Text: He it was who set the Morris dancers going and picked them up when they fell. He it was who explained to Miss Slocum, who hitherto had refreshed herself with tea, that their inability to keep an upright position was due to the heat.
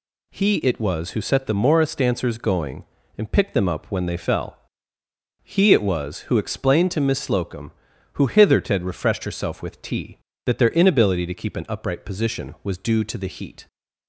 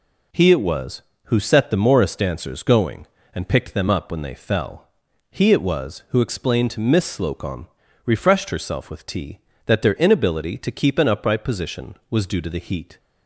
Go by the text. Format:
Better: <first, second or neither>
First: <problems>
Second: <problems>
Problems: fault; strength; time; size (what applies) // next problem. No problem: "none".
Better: first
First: none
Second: skips "who hitherto had"; at 7.8 s